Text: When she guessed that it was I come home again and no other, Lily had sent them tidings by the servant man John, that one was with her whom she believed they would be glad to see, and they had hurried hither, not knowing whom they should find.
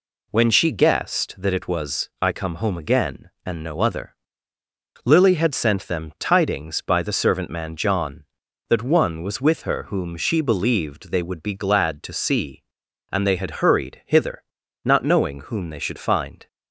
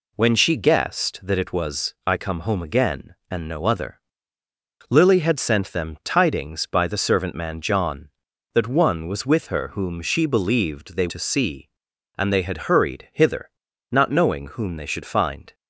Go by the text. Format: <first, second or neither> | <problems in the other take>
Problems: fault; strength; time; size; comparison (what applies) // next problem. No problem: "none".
first | skips "would be glad"; at 11.0 s